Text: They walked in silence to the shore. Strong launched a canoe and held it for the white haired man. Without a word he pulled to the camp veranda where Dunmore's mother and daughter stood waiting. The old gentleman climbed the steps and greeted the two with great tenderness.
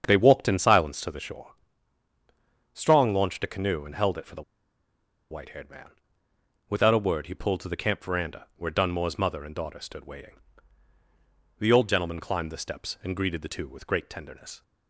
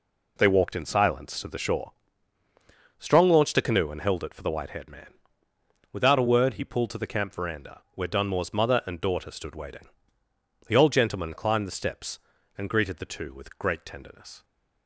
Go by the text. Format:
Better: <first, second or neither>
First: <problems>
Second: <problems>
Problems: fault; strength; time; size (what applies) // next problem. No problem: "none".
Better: second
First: starts louder than the rest; strong; until 1.0 s; 7.5 dB // pauses between "the" and "white"; noticeable; at 4.4 s; 0.89 s long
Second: none